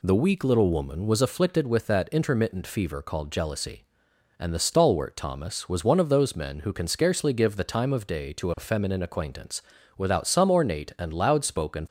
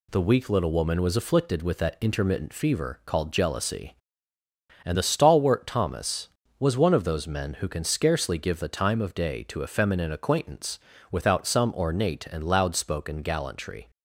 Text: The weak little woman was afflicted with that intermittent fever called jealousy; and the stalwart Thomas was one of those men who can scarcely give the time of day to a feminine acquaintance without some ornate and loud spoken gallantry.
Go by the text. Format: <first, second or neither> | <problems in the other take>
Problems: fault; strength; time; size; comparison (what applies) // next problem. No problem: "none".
second | pauses between "acquaintance" and "without"; at 9.6 s; 0.38 s long; slight in the second // stops before "gallantry"; at 11.8 s